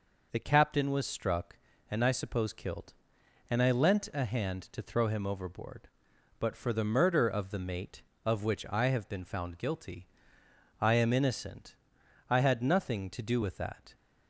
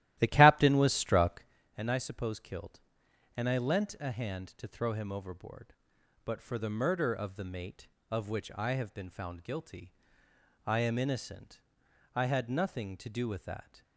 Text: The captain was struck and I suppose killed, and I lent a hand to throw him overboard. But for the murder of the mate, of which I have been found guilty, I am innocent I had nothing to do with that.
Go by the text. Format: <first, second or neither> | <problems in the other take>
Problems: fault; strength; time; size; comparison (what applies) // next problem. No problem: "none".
first | starts louder than the rest; strong; until 1.6 s; 14 dB // pauses between "innocent" and "I"; noticeable; at 11.6 s; 0.52 s long; noticeable in the first